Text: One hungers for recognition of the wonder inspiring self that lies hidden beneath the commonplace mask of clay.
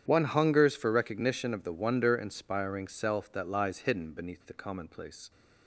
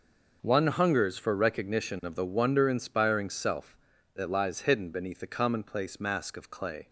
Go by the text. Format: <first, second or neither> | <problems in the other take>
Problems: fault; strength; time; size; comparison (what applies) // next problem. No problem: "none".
second | starts louder than the rest; strong; until 1.0 s; 9 dB // stops before "mask of clay"; at 5.3 s